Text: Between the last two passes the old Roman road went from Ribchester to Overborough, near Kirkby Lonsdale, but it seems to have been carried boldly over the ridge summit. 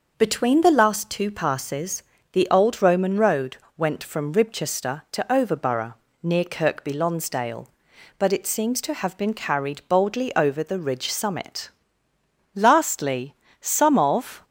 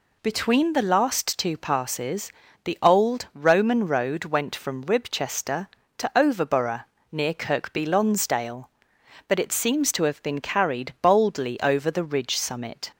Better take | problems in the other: second | pauses between "passes" and "the"; slight; at 2.0 s; 0.30 s long; slight in the second // pauses between "road" and "went"; slight; at 3.5 s; 0.20 s long // goes on to say "Lastly some of"; strong; from 12.5 s on; 1.9 s long

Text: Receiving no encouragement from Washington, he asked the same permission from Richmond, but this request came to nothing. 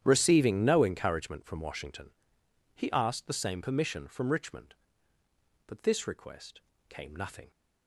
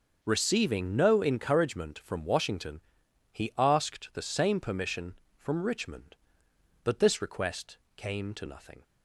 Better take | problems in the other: second | starts louder than the rest; strong; until 1.0 s; 10 dB; also in the second // pauses between "request" and "came"; slight; at 6.6 s; 0.26 s long; slight in the second // skips "to"; at 7.1 s

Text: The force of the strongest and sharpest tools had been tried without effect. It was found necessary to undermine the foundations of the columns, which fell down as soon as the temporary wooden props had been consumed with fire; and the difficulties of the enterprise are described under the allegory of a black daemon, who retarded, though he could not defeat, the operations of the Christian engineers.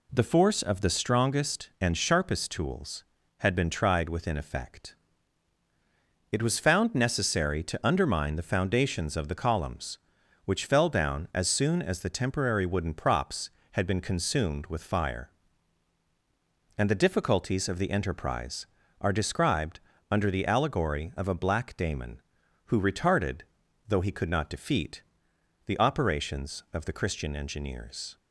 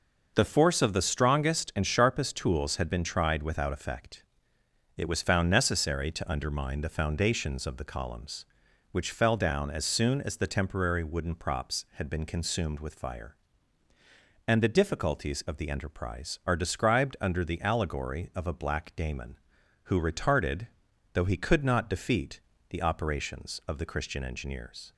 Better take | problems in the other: second | says "within" for "without"; at 4.0 s // pauses between "described" and "under"; slight; at 19.7 s; 0.30 s long

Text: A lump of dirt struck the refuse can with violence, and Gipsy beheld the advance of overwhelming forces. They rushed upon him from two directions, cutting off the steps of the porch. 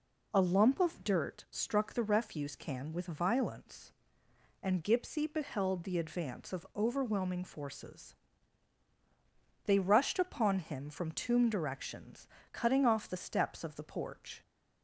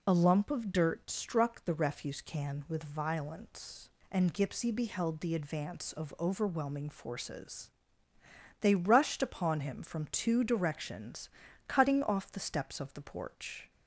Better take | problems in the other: second | says "tomb" for "two"; at 11.1 s

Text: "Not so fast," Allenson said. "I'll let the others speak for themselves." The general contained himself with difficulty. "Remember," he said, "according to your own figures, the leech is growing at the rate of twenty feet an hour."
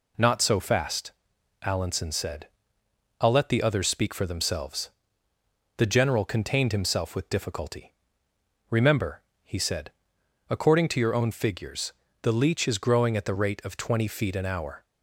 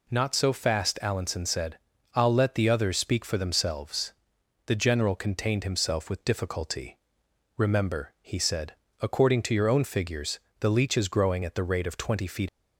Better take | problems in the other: first | stops before "an hour"; at 12.4 s

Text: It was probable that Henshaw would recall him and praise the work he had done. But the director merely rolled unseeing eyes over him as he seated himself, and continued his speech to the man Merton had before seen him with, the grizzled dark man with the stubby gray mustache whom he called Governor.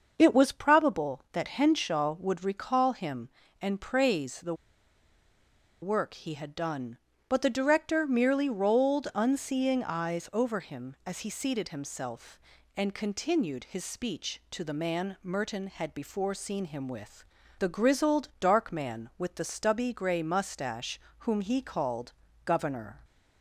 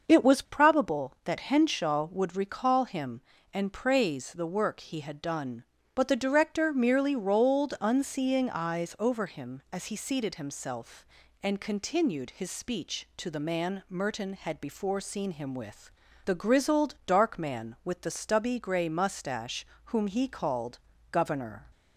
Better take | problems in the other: second | starts louder than the rest; until 1.1 s; 6 dB; also in the second // pauses between "the" and "work"; strong; at 4.5 s; 1.2 s long // pauses between "mustache" and "whom"; slight; at 20.9 s; 0.20 s long; slight in the second // pauses between "called" and "Governor"; slight; at 22.1 s; 0.32 s long; slight in the second

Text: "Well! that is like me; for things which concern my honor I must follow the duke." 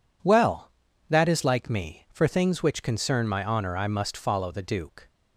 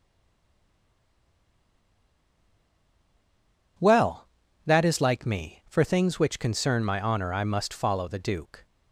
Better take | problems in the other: first | stays silent before the first word; strong; until 3.7 s; 3.7 s long

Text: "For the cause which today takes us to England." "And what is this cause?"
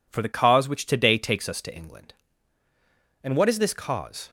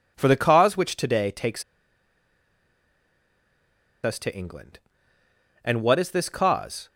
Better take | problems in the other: first | pauses between "takes" and "us"; strong; at 1.6 s; 2.4 s long

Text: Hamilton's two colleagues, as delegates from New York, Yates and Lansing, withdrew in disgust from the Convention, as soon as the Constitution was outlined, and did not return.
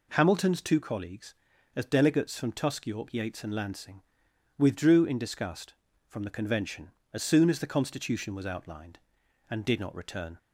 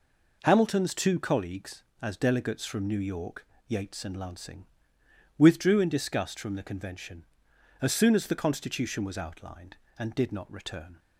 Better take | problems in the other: second | says "Tusk" for "New"; at 2.5 s

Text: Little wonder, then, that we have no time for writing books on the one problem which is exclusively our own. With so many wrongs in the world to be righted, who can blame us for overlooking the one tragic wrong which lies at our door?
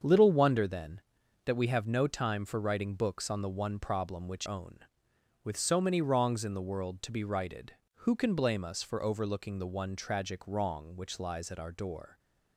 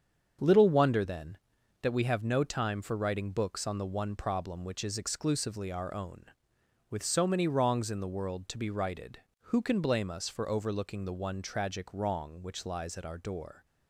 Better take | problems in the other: second | starts louder than the rest; until 1.4 s; 7 dB; strong in the second // skips "is exclusively our"; at 4.4 s

